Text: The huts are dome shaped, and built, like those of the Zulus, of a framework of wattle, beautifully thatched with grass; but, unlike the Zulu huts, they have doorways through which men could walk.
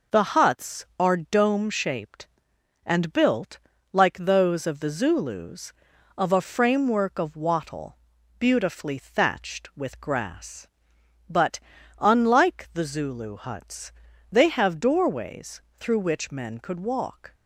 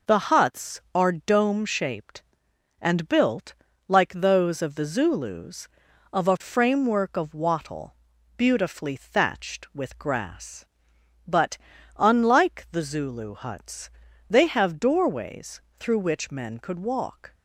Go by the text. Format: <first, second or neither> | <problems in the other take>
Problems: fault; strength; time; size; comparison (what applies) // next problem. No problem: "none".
neither | pauses between "doorways" and "through"; slight; the same in both